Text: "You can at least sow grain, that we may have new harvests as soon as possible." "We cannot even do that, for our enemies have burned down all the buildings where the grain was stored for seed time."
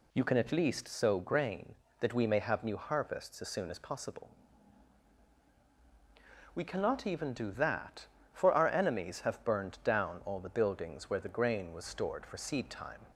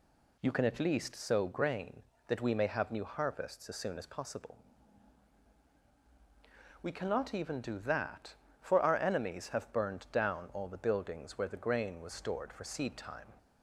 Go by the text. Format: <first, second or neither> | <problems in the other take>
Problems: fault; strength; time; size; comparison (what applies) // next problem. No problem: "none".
neither | none